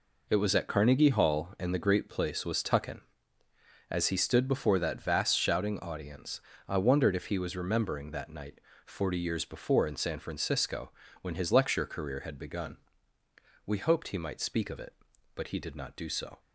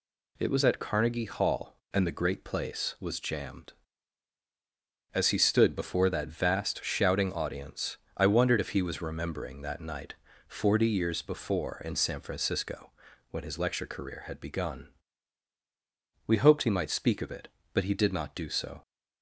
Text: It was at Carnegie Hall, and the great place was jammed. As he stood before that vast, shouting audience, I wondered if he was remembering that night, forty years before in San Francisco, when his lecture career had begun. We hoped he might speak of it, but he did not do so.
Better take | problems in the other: second | says "tuckin" for "jammed"; at 2.6 s

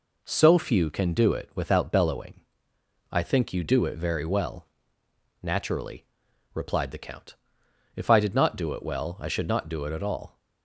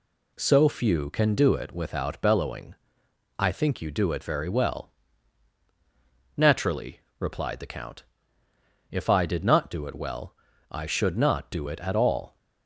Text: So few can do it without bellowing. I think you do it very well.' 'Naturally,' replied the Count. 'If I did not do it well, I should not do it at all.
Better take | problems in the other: neither | none

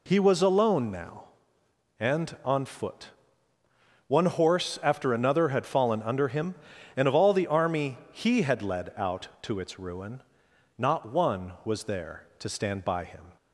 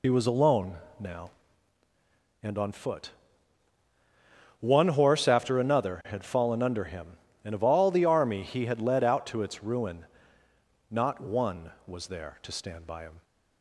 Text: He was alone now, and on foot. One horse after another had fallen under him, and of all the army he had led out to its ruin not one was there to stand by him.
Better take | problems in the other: first | loses the start of "He"; at 0.0 s; 50 ms // pauses between "alone" and "now"; slight; at 0.7 s; 0.22 s long // pauses between "ruin" and "not"; noticeable; at 10.0 s; 0.86 s long; noticeable in the first

